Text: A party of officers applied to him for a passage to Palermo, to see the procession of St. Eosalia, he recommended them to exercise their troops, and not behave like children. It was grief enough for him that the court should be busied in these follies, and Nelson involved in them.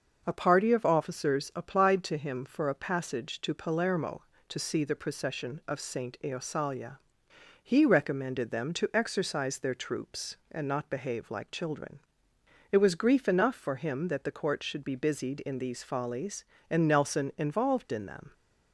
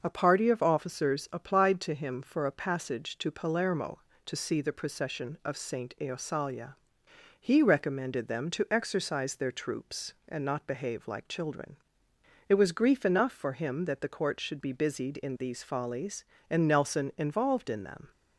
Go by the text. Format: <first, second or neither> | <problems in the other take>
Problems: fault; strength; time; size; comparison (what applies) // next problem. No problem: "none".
neither | starts louder than the rest; noticeable; the same in both